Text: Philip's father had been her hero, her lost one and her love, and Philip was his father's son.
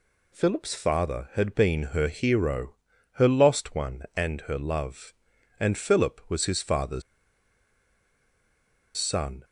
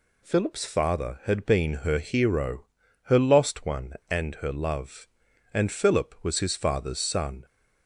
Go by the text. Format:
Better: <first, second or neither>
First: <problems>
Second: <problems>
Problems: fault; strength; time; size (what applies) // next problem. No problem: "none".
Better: second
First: pauses between "father's" and "son"; strong; at 7.0 s; 1.9 s long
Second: none